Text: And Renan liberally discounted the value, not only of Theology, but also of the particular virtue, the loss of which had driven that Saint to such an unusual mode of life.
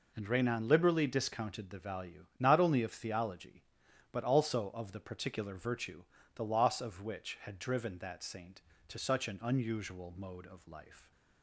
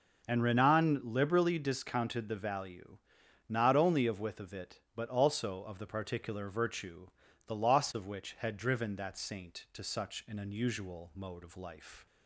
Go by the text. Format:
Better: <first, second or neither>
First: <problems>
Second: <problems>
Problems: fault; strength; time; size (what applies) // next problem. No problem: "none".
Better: first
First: none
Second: says "Withovit" for "Theology"; at 4.2 s